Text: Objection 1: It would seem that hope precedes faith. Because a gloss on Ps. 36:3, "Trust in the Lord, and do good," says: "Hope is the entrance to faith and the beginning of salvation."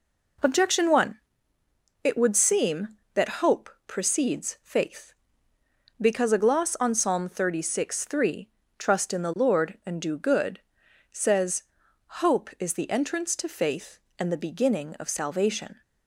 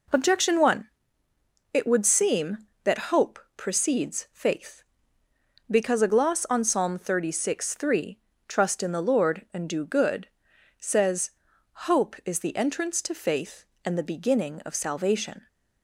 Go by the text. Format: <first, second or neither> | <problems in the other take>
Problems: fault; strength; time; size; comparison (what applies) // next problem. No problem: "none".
neither | pauses between "hope" and "precedes"; slight; the same in both